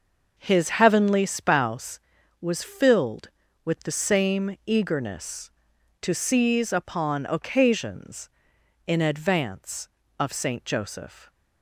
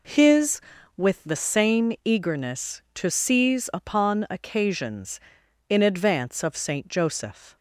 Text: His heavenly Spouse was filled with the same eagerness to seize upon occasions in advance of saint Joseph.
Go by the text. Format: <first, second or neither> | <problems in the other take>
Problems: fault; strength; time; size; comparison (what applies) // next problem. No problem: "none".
first | skips "heavenly Spouse was filled"; at 0.7 s